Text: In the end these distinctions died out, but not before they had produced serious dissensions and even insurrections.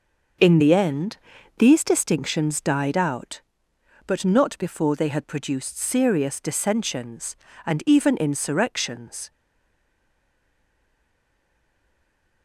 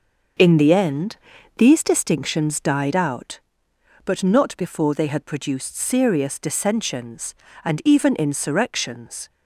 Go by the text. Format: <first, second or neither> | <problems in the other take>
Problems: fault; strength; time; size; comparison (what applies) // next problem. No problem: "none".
second | starts louder than the rest; until 1.8 s; 6 dB; also in the second // pauses between "end" and "these"; at 1.1 s; 0.42 s long; also in the second // stays silent after the last word; strong; from 9.3 s on; 3.1 s long